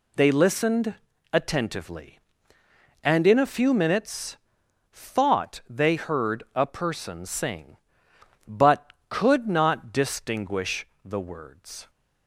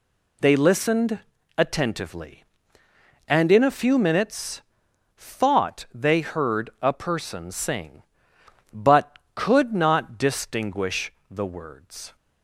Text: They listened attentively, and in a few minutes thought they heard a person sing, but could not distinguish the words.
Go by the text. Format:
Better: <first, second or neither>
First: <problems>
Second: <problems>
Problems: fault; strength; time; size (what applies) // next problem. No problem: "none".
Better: neither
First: pauses between "listened" and "attentively"; at 0.9 s; 0.38 s long // pauses between "minutes" and "thought"; noticeable; at 4.3 s; 0.56 s long // pauses between "distinguish" and "the"; slight; at 10.8 s; 0.20 s long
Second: pauses between "listened" and "attentively"; at 1.1 s; 0.38 s long // pauses between "minutes" and "thought"; noticeable; at 4.6 s; 0.56 s long // pauses between "distinguish" and "the"; slight; at 11.1 s; 0.20 s long